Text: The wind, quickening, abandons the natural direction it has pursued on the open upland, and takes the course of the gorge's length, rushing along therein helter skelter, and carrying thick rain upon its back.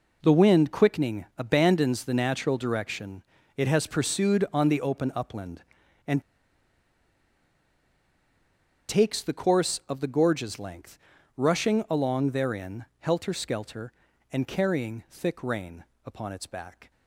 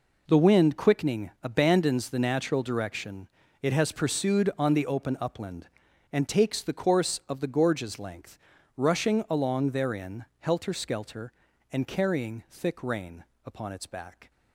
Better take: second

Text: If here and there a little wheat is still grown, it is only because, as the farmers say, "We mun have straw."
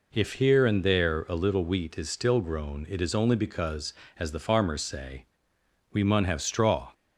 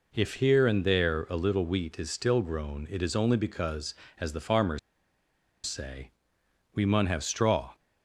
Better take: first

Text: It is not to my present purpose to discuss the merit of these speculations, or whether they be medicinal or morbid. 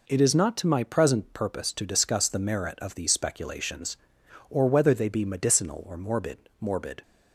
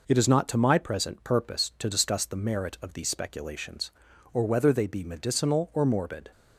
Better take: second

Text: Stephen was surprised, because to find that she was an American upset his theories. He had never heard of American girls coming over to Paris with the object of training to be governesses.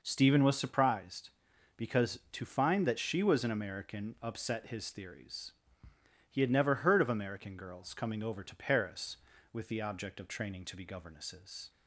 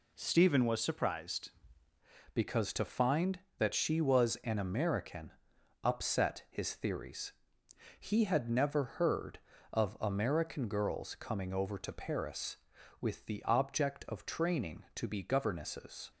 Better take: first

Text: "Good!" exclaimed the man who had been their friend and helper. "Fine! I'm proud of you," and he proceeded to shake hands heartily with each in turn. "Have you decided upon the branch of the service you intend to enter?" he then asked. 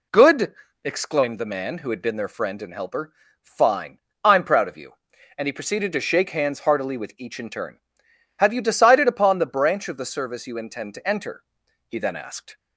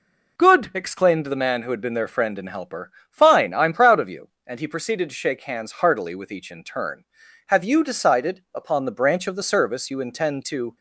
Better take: first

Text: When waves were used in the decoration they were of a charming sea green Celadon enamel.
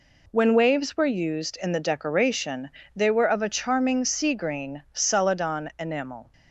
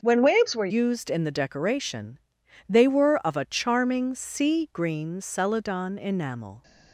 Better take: first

